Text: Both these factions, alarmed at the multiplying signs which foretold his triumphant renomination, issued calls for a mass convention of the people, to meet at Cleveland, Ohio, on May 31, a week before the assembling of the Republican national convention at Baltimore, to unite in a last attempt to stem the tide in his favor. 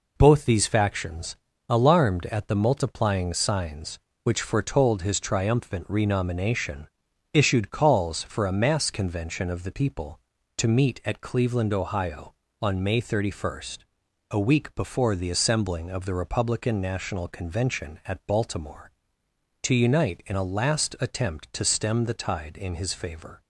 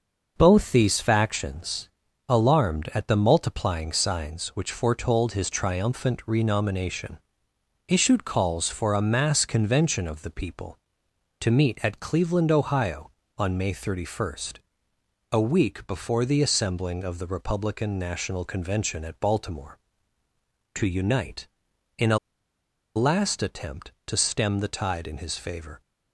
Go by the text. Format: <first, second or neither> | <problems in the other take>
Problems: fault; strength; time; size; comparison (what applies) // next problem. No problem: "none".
first | starts louder than the rest; noticeable; until 1.3 s; 6 dB // pauses between "a" and "last"; noticeable; at 22.1 s; 0.77 s long